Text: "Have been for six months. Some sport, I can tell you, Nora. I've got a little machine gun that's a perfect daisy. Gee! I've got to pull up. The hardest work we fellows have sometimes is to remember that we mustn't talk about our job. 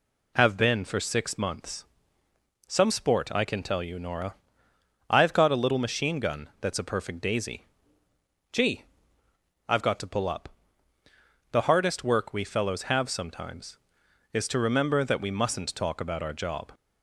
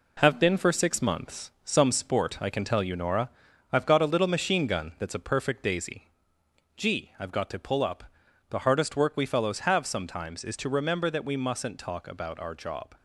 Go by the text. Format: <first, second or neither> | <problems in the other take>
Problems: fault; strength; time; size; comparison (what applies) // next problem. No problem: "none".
first | gets quieter; noticeable; throughout; 5 dB